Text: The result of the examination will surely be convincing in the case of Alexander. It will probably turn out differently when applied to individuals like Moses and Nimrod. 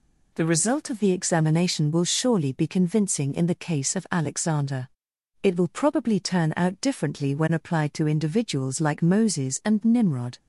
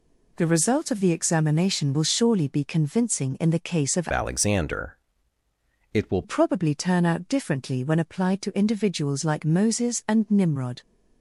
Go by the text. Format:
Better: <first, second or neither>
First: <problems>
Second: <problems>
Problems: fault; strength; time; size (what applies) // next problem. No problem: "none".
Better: first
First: none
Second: changes voice from "Alexander" to "will"; from 4.1 to 6.2 s; 2.1 s long